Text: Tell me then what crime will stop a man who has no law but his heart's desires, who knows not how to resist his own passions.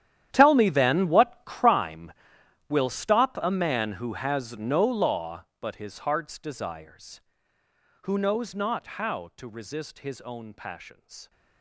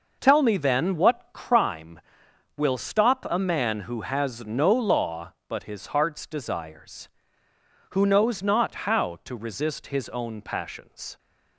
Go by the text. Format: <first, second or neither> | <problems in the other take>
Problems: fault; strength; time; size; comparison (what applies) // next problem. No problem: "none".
second | gets quieter; strong; throughout; 17 dB